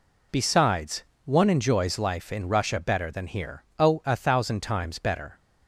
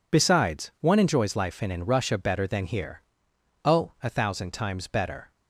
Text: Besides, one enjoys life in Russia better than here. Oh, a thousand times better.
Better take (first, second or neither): first